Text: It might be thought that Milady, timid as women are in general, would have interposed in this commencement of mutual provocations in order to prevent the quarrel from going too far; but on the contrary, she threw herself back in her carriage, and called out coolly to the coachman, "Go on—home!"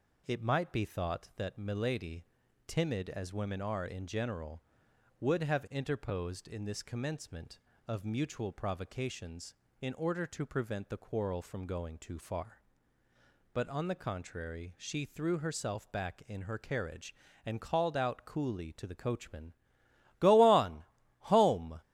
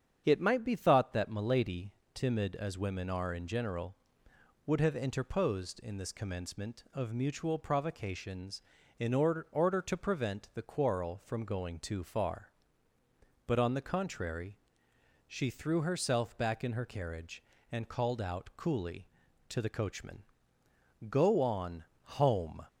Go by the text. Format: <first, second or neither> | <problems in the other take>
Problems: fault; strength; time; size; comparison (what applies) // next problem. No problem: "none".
first | starts louder than the rest; strong; until 1.2 s; 8 dB // says "order" twice; at 9.4 s